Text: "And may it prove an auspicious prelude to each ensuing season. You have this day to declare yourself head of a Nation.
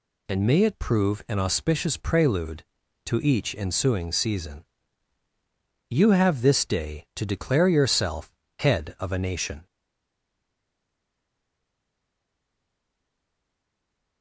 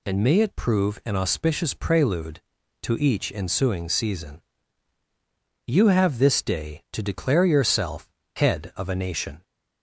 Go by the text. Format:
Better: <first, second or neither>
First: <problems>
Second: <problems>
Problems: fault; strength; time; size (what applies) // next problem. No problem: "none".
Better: second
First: pauses between "yourself" and "head"; slight; at 8.3 s; 0.26 s long // stays silent after the last word; strong; from 9.6 s on; 4.6 s long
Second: pauses between "yourself" and "head"; slight; at 8.0 s; 0.26 s long